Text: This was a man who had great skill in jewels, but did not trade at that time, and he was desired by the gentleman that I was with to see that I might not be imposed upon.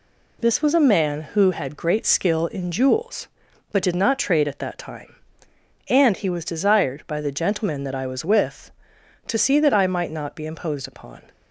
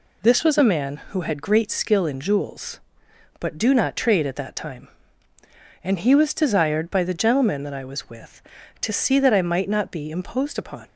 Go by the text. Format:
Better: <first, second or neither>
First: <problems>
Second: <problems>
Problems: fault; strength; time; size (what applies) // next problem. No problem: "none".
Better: first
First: none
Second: says "do" for "did"; at 3.5 s